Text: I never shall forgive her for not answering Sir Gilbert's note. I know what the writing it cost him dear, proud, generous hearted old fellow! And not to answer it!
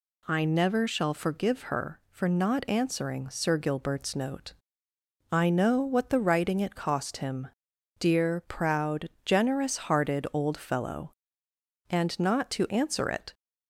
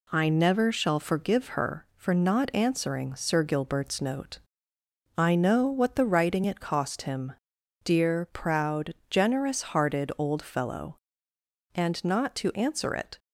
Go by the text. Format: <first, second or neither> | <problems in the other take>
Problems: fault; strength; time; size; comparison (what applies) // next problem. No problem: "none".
first | gets quieter; throughout; 3.5 dB // pauses between "him" and "dear"; noticeable; at 7.3 s; 0.50 s long; noticeable in the first